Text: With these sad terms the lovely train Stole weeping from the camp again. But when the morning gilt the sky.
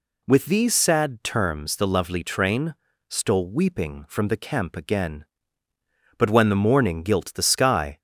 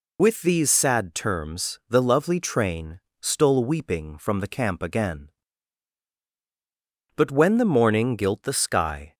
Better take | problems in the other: first | loses the start of "With"; at 0.1 s; 50 ms // pauses between "train" and "Stole"; slight; at 2.9 s; 0.26 s long; slight in the first

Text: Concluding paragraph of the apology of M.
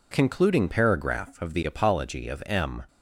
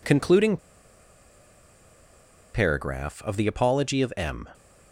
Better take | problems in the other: first | pauses between "Concluding" and "paragraph"; strong; at 0.5 s; 1.9 s long

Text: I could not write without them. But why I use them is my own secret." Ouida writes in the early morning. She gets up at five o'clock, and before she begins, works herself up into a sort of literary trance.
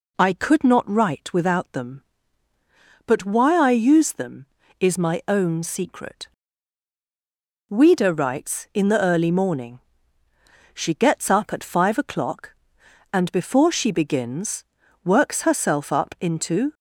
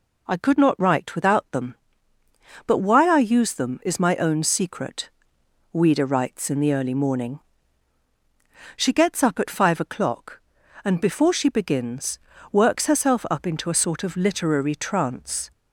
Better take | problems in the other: second | stops before "a sort of literary trance"; at 16.7 s

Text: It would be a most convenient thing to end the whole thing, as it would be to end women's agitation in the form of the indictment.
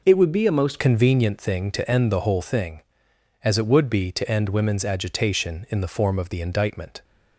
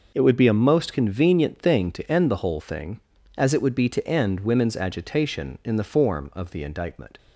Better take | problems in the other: second | changes voice at "convenient"; from 0.7 s on; 6.3 s long

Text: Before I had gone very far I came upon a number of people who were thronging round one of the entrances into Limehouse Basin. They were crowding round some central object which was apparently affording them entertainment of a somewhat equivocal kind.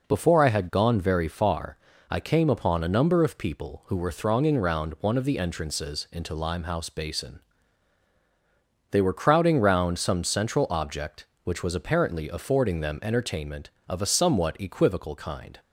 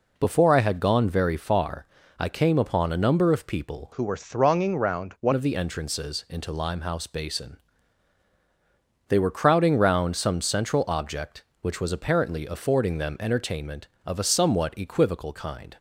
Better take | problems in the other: first | pauses between "far" and "I"; slight; at 1.8 s; 0.32 s long; slight in the first // changes voice from "who" to "one"; from 3.9 to 5.3 s; 1.4 s long

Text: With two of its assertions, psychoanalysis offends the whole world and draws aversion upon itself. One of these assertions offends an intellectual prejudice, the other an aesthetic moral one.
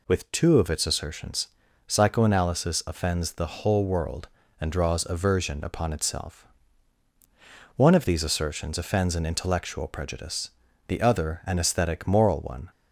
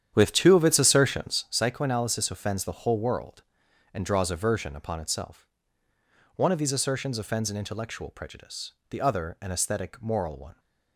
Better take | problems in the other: first | starts louder than the rest; strong; until 1.6 s; 9.5 dB

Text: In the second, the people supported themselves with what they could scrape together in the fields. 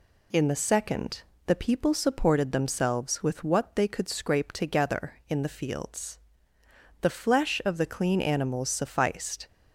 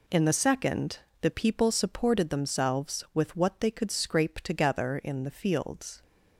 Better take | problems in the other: second | goes on to say "The flesh of the clean animals sufficed"; strong; from 7.0 s on; 2.4 s long

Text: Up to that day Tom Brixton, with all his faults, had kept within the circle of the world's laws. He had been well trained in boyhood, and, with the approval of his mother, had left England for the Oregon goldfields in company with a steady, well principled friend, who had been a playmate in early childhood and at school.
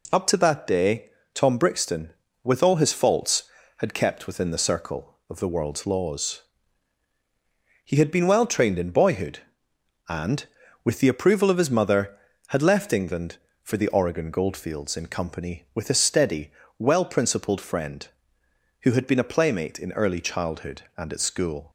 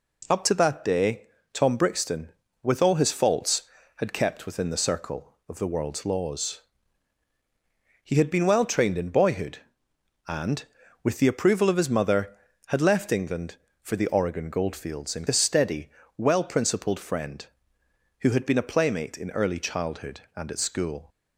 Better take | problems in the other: first | pauses between "day" and "Tom"; slight; at 1.2 s; 0.28 s long; slight in the first // skips "company with"; at 15.2 s

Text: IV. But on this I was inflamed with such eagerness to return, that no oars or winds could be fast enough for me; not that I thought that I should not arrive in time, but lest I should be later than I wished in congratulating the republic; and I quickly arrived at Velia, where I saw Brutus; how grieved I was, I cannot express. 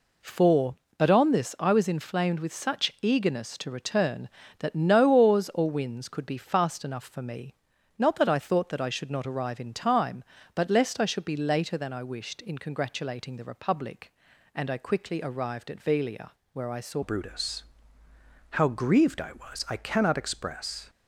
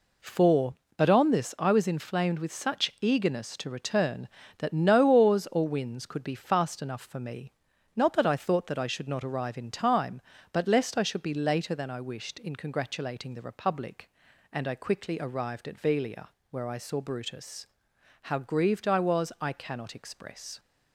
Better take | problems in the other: second | changes voice at "Brutus"; from 17.0 s on; 3.8 s long

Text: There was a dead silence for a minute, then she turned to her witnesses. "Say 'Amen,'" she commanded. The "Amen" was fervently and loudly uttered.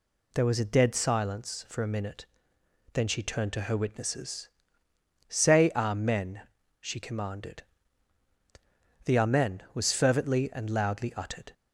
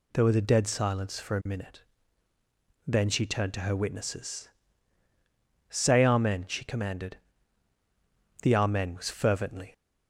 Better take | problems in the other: first | stops before "and loudly uttered"; at 9.7 s

